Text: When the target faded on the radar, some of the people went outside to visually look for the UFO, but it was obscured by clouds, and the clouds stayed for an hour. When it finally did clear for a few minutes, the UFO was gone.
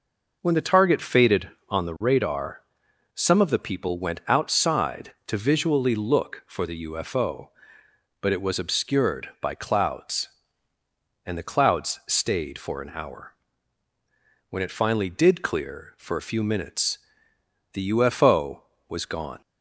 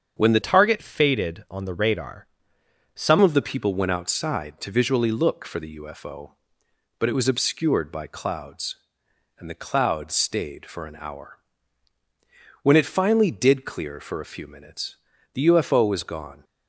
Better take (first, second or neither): first